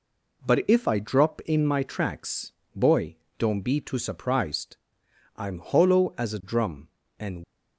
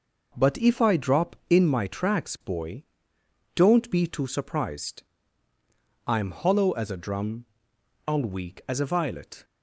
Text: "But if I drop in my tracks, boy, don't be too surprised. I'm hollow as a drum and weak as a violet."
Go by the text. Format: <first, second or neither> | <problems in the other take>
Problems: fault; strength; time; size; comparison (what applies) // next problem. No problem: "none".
second | stops before "weak as a violet"; at 7.4 s